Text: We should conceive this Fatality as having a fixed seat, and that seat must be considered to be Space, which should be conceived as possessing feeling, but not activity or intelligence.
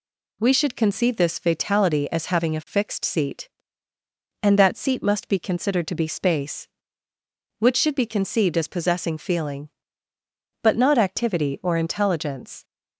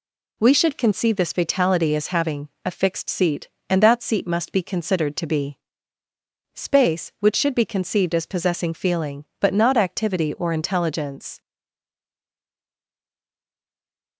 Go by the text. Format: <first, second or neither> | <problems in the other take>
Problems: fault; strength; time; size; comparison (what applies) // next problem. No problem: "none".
first | pauses between "be" and "Space"; noticeable; at 5.5 s; 0.98 s long // stays silent after the last word; strong; from 11.4 s on; 2.7 s long